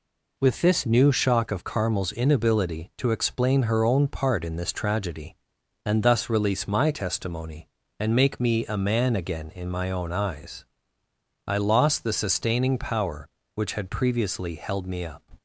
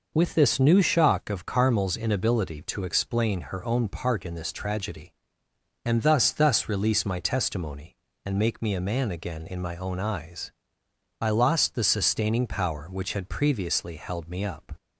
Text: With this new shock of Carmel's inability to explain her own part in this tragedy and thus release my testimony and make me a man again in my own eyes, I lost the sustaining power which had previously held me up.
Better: first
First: none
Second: says "thus" twice; at 6.3 s

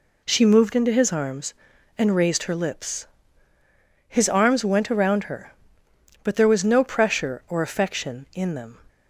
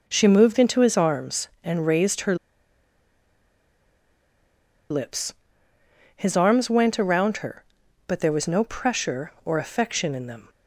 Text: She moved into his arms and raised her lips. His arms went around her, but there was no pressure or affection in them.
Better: first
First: none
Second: pauses between "her" and "lips"; strong; at 2.3 s; 2.5 s long

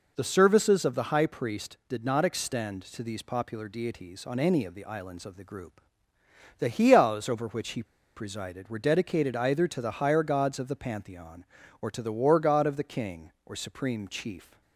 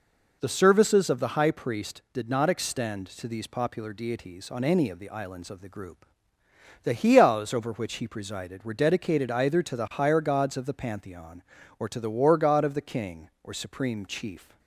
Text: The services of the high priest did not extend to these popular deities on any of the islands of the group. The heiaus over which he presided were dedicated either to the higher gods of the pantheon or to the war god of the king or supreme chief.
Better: second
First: pauses between "he" and "presided"; slight; at 7.8 s; 0.32 s long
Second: none

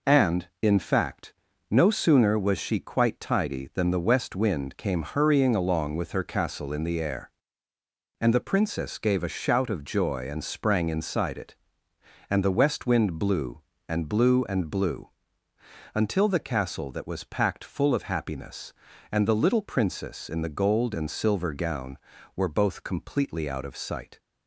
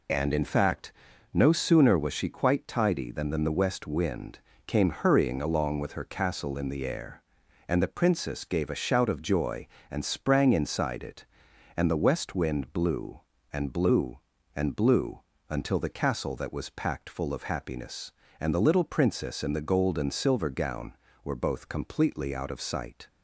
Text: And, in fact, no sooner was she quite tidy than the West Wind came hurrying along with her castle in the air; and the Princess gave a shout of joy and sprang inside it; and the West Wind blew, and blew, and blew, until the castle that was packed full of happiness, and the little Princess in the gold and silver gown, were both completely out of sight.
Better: first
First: none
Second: says "than" twice; at 3.2 s // pauses between "Wind" and "came"; slight; at 4.3 s; 0.28 s long

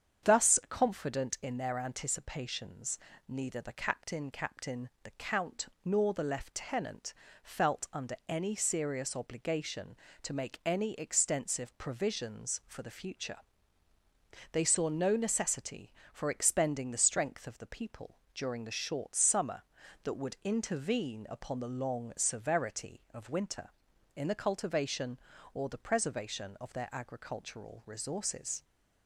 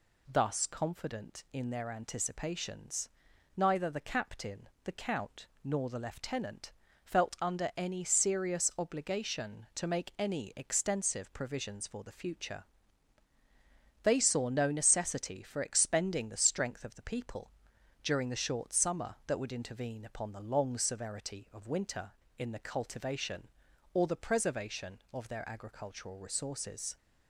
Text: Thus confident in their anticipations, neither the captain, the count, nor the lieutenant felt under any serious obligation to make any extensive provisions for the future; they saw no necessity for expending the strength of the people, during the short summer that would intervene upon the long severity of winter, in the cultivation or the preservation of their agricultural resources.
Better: second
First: starts louder than the rest; strong; until 1.3 s; 8 dB // says "captain" twice; at 4.3 s // pauses between "lieutenant" and "felt"; slight; at 7.1 s; 0.30 s long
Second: pauses between "lieutenant" and "felt"; slight; at 6.7 s; 0.32 s long

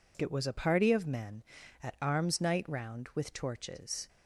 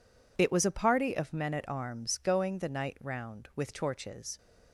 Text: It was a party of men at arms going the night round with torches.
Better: second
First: skips "going the"; at 2.3 s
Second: none

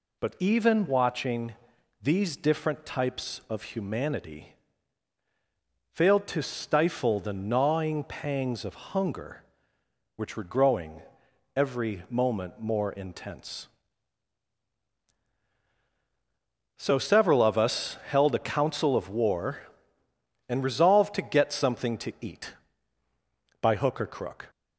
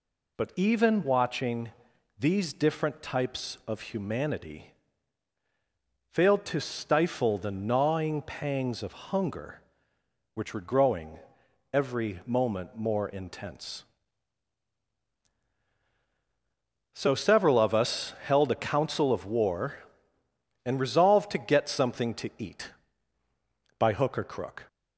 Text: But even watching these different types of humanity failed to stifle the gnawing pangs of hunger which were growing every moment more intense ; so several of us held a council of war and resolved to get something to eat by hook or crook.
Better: neither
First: pauses between "watching" and "these"; noticeable; at 1.5 s; 0.50 s long // pauses between "humanity" and "failed"; strong; at 4.5 s; 1.3 s long // pauses between "growing" and "every"; noticeable; at 11.0 s; 0.54 s long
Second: pauses between "watching" and "these"; noticeable; at 1.6 s; 0.50 s long // pauses between "humanity" and "failed"; strong; at 4.7 s; 1.3 s long // pauses between "growing" and "every"; noticeable; at 11.1 s; 0.54 s long

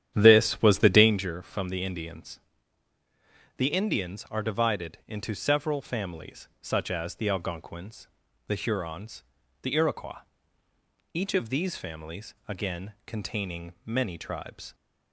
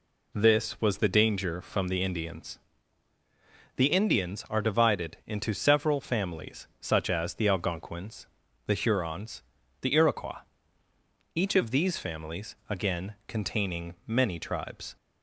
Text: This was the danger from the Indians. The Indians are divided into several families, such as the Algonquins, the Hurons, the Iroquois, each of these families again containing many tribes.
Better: second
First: starts louder than the rest; strong; until 1.3 s; 10.5 dB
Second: none

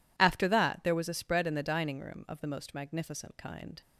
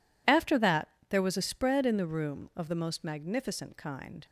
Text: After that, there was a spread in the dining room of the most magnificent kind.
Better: first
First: none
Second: skips "dining"; at 2.0 s

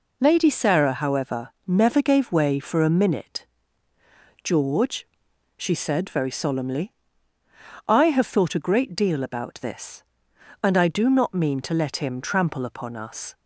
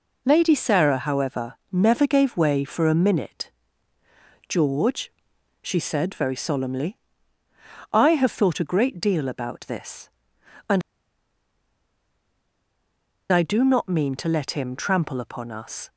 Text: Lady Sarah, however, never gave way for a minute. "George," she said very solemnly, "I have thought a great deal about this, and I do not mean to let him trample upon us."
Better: first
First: none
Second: pauses between "and" and "I"; strong; at 10.8 s; 2.5 s long

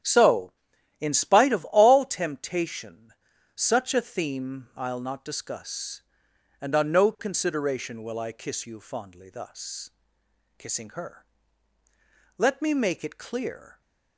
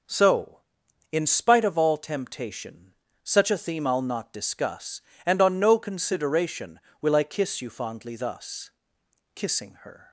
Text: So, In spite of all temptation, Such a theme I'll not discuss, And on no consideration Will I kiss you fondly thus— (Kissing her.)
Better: second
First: starts louder than the rest; strong; until 1.4 s; 10 dB // goes on to say "Let me make it clear"; from 12.3 s on; 1.4 s long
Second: none

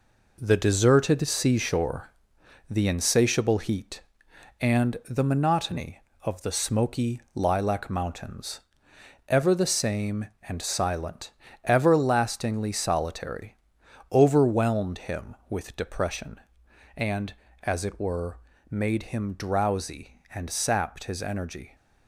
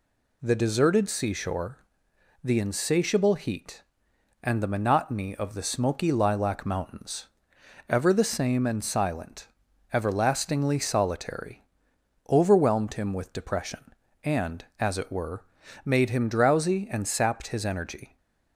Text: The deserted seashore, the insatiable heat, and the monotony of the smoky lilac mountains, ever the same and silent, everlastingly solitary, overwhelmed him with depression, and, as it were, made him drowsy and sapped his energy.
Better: second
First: gets quieter; throughout; 6.5 dB // pauses between "smoky" and "lilac"; slight; at 7.1 s; 0.16 s long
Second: none

